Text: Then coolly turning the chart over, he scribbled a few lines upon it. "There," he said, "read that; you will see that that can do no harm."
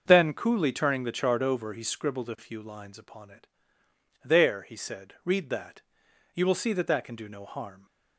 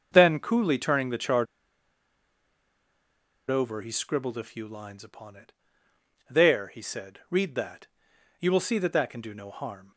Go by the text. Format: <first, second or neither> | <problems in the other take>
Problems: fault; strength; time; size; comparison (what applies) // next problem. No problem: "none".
first | starts louder than the rest; until 1.1 s; 6.5 dB; also in the first // pauses between "chart" and "over"; strong; at 1.4 s; 2.0 s long